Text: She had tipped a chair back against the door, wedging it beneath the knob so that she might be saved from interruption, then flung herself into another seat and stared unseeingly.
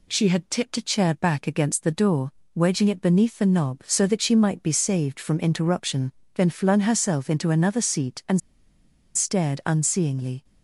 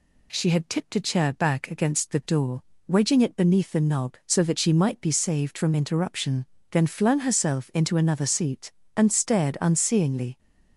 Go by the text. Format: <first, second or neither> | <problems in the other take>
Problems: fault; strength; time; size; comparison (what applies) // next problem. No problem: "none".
second | pauses between "and" and "stared"; noticeable; at 8.4 s; 0.75 s long